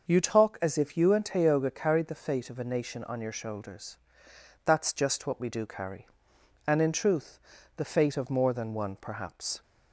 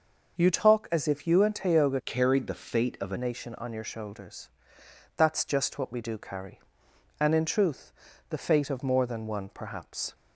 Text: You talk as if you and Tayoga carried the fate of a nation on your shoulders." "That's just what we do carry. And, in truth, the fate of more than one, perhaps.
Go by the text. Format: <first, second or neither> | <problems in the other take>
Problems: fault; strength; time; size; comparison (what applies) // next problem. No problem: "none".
first | starts louder than the rest; noticeable; until 1.4 s; 6 dB // changes voice from "carried" to "a"; from 2.0 to 3.1 s; 1.1 s long